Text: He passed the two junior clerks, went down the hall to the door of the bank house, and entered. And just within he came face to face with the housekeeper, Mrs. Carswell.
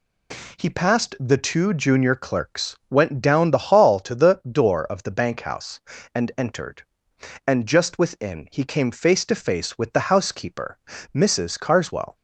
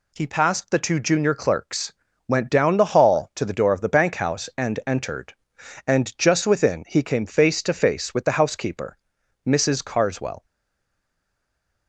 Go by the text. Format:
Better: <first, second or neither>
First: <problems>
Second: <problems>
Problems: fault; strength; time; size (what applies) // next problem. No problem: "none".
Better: first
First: none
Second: stays silent after the last word; noticeable; from 10.4 s on; 1.4 s long